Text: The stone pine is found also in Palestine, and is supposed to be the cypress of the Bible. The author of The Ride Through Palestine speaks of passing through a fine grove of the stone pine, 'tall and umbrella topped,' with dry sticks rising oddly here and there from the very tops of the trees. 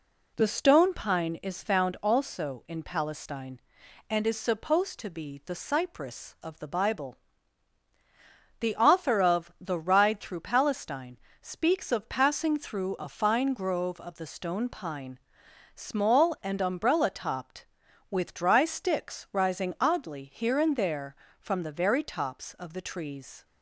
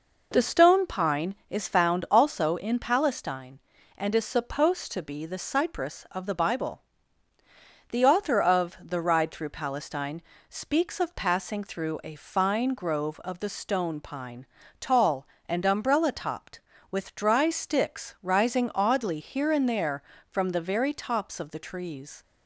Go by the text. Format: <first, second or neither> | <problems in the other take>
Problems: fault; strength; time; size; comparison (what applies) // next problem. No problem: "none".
second | pauses between "Palestine" and "speaks"; slight; at 11.1 s; 0.24 s long; slight in the second // says "small" for "tall"; at 15.7 s